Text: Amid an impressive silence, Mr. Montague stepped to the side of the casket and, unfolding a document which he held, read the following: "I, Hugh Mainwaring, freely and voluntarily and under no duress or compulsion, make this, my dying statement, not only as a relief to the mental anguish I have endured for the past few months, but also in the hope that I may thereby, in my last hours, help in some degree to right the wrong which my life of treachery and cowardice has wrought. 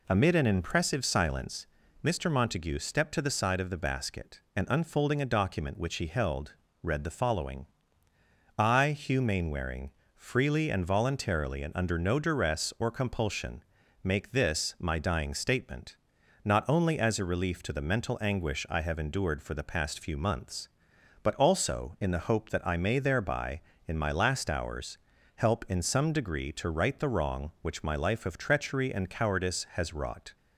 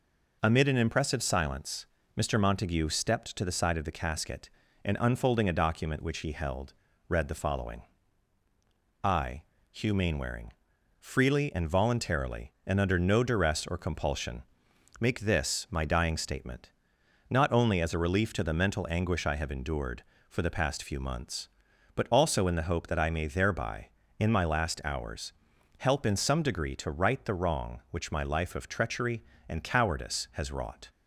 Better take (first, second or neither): second